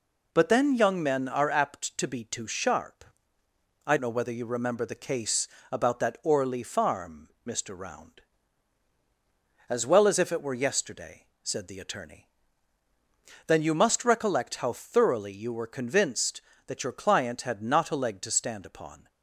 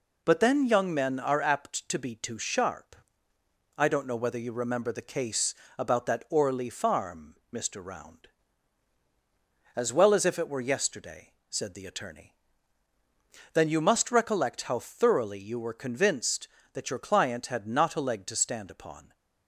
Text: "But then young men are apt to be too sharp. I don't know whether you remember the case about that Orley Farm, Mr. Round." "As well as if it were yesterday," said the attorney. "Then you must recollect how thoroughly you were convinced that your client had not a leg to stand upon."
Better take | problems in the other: second | skips "don't"; at 3.9 s // pauses between "case" and "about"; slight; at 5.4 s; 0.22 s long; slight in the second

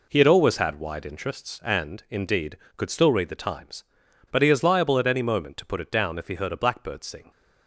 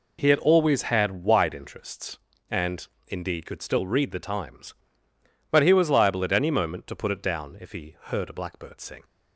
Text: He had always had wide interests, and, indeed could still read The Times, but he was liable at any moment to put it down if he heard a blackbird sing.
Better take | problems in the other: second | says "is" for "was"; at 4.5 s

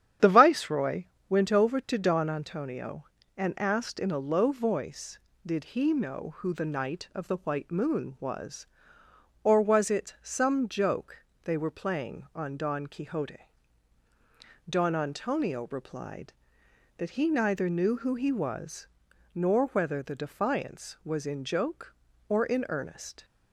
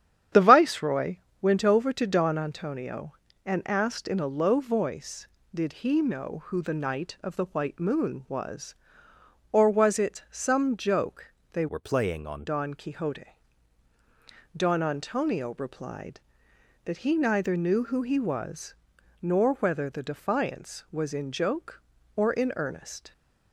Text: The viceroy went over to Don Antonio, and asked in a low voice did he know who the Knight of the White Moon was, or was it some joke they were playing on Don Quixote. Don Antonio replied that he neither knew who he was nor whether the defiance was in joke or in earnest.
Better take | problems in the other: first | starts louder than the rest; strong; until 1.5 s; 9.5 dB; strong in the first // pauses between "viceroy" and "went"; slight; at 1.1 s; 0.24 s long; slight in the first // pauses between "joke" and "they"; slight; at 11.2 s; 0.24 s long; slight in the first // changes voice from "were" to "on"; from 11.6 to 12.4 s; 0.8 s long // pauses between "was" and "nor"; noticeable; at 18.7 s; 0.48 s long; noticeable in the first

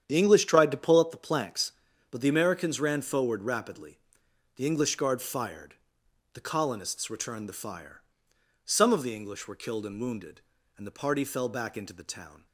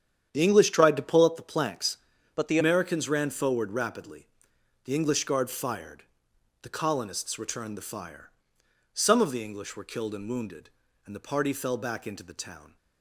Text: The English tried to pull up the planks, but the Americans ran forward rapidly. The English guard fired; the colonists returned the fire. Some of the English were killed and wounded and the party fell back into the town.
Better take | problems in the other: first | starts louder than the rest; strong; until 1.3 s; 9 dB; strong in the first // changes voice from "but" to "the"; from 2.3 to 2.5 s; 0.2 s long

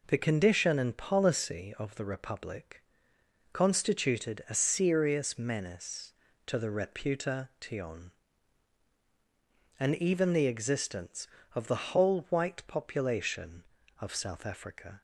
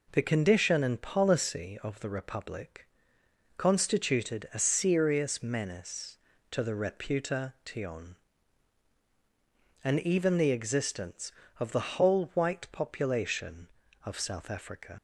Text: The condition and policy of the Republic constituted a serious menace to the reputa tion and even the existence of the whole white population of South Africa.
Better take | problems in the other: first | pauses between "Republic" and "constituted"; noticeable; at 2.8 s; 0.70 s long; noticeable in the first // leaves "Africa" unfinished; at 14.9 s; 70 ms

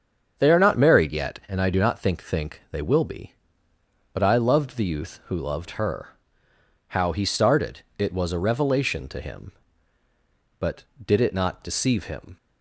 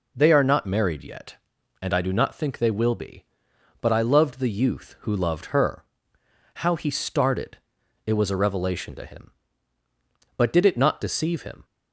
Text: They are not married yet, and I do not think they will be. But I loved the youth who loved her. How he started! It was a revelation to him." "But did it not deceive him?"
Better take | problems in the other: second | starts louder than the rest; until 1.3 s; 7 dB // says "think" twice; at 2.2 s

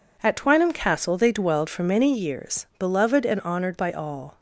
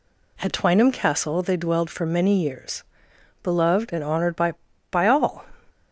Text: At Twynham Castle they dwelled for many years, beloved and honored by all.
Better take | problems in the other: first | says "by" twice; at 4.9 s

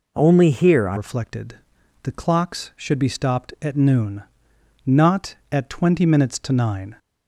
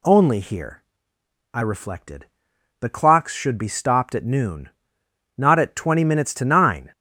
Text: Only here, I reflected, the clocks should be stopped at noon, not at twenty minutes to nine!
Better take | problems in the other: second | changes voice at "reflected"; from 0.9 s on; 6.0 s long

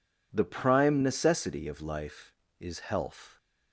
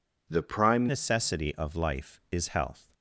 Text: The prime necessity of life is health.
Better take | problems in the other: first | changes voice at "necessity"; from 0.8 s on; 2.1 s long

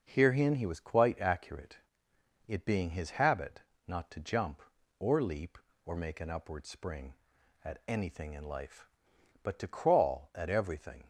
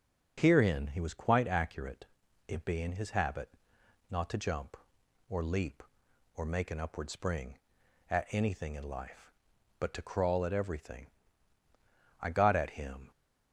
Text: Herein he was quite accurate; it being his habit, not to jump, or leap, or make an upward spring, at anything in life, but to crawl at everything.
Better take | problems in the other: first | goes on to say "I got at him"; noticeable; from 12.2 s on; 0.88 s long

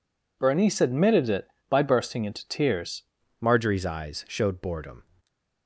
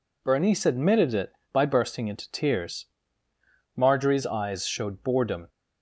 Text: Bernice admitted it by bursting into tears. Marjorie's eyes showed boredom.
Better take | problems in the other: second | changes voice at "Marjorie's"; from 3.4 s on; 1.6 s long // stays silent after the last word; slight; from 5.0 s on; 0.6 s long

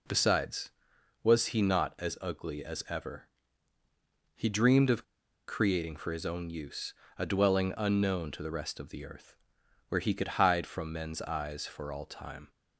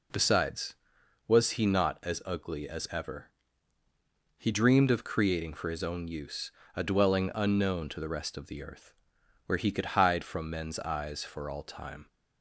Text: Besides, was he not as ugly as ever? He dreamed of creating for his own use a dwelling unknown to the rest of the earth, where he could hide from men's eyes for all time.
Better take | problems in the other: second | pauses between "of" and "creating"; at 5.0 s; 0.45 s long // pauses between "use" and "a"; slight; at 6.9 s; 0.26 s long; slight in the second

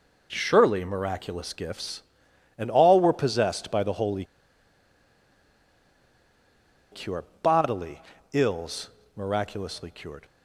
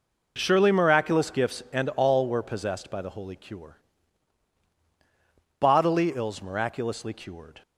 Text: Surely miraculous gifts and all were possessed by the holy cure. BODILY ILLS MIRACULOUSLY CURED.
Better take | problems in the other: second | pauses between "holy" and "cure"; strong; at 4.2 s; 2.6 s long // pauses between "BODILY" and "ILLS"; slight; at 8.0 s; 0.32 s long // pauses between "ILLS" and "MIRACULOUSLY"; slight; at 8.8 s; 0.26 s long

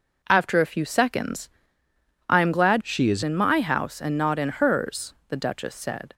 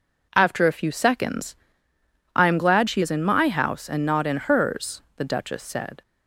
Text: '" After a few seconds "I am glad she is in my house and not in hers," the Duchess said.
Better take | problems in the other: second | pauses between "seconds" and "I"; noticeable; at 1.4 s; 0.80 s long; noticeable in the second // changes voice from "she" to "is"; from 2.8 to 3.2 s; 0.4 s long

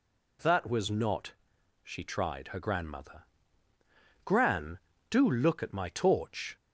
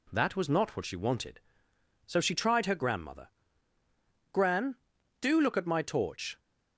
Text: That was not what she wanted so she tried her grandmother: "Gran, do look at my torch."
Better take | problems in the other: second | skips "what she wanted so"; at 1.5 s

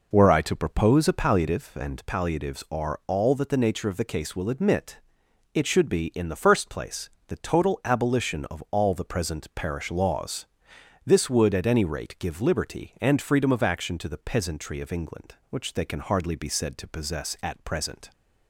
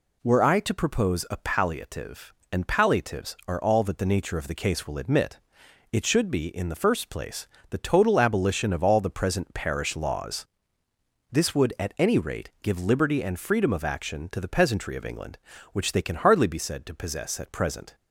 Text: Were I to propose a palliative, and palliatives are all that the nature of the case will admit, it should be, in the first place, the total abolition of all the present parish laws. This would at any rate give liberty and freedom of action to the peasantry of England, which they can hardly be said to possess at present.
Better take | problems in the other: second | starts louder than the rest; noticeable; until 1.6 s; 5 dB

